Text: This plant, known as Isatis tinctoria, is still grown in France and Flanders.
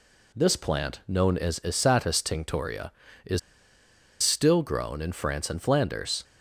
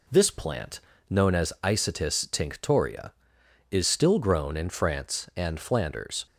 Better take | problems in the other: second | pauses between "is" and "still"; noticeable; at 3.3 s; 0.83 s long

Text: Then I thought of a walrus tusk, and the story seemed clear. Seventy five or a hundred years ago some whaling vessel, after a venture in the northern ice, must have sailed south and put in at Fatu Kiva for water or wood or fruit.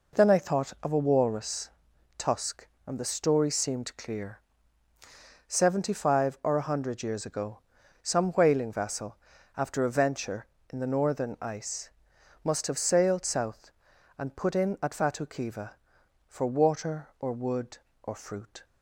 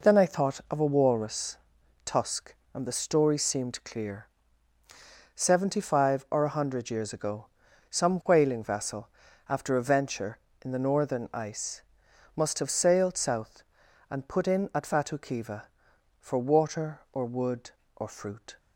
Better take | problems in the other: neither | pauses between "walrus" and "tusk"; noticeable; the same in both // pauses between "ago" and "some"; noticeable; the same in both

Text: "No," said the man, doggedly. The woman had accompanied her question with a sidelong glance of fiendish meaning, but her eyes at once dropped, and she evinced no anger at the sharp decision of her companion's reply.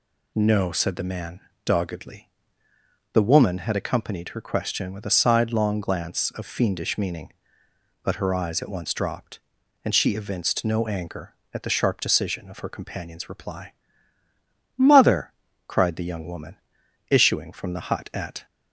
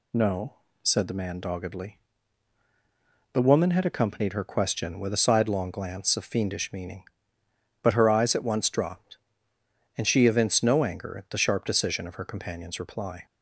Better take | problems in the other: second | goes on to say "Mother cried the young woman issuing from the hut at"; strong; from 14.7 s on; 3.6 s long

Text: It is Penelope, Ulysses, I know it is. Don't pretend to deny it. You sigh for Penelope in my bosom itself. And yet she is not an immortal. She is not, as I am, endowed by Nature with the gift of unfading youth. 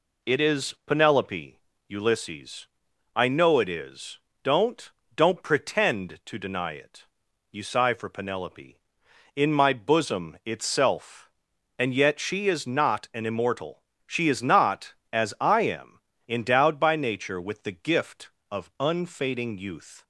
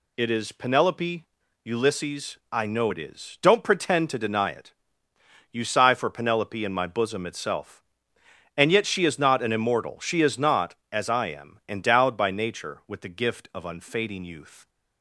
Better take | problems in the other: second | says "Don't" twice; at 5.1 s

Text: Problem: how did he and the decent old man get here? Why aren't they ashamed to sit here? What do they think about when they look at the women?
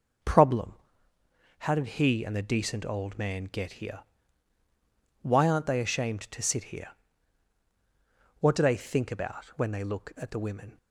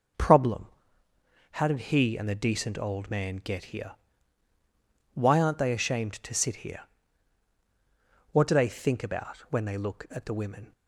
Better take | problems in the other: neither | none

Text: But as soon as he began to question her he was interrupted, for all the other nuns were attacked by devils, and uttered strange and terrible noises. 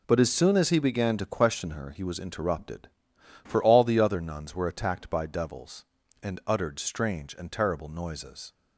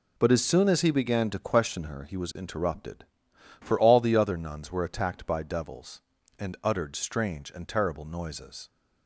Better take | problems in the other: neither | none

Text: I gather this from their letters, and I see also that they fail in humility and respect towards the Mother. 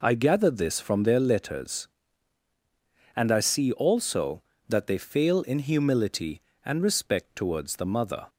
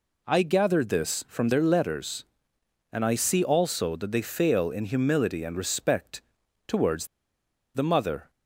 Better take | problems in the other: first | pauses between "respect" and "towards"; noticeable; at 6.2 s; 0.48 s long // pauses between "towards" and "the"; noticeable; at 7.0 s; 0.67 s long

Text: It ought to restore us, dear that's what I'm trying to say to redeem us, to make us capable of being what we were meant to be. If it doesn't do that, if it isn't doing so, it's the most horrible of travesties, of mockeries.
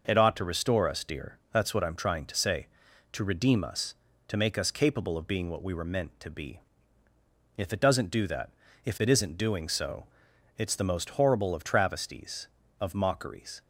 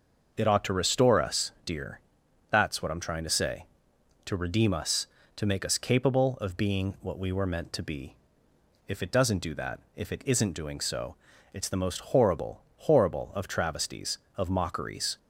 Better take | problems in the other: first | starts louder than the rest; noticeable; until 1.3 s; 6 dB // pauses between "dear" and "that's"; noticeable; at 1.9 s; 0.52 s long // says "horrible" twice; at 12.7 s

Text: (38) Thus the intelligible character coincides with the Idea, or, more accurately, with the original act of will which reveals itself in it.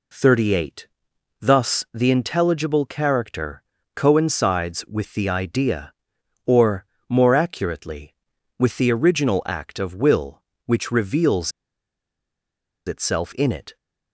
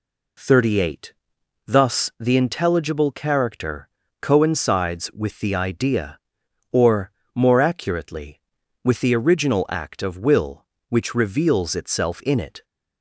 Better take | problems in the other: second | pauses between "character" and "coincides"; slight; at 3.6 s; 0.34 s long; slight in the second // pauses between "reveals" and "itself"; strong; at 11.5 s; 1.3 s long

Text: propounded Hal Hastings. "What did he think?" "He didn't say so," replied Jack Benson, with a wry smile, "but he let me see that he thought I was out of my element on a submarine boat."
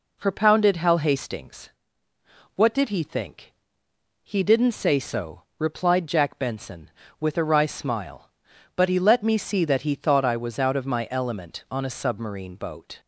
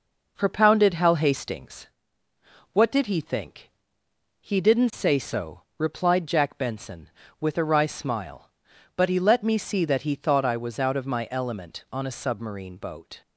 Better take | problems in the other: first | gets quieter; slight; throughout; 3.5 dB

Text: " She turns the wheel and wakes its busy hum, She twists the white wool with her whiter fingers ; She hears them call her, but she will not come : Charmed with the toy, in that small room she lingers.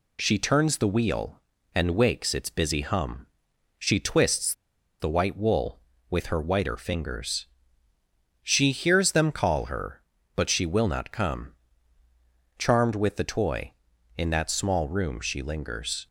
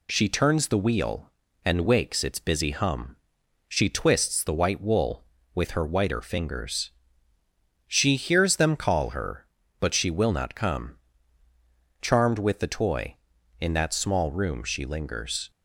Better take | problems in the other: second | pauses between "twists" and "the"; noticeable; at 4.5 s; 0.48 s long

